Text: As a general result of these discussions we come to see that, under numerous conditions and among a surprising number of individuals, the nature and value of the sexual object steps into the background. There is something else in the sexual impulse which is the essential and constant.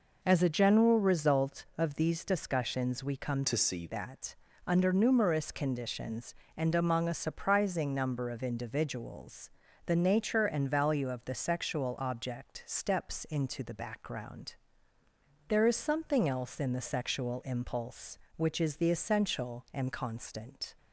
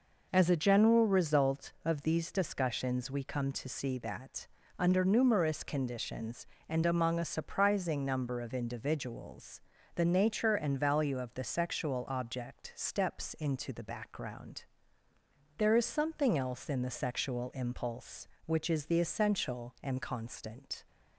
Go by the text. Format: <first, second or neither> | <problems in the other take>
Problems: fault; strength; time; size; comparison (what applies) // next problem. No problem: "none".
second | changes voice from "to" to "see"; from 3.4 to 3.8 s; 0.4 s long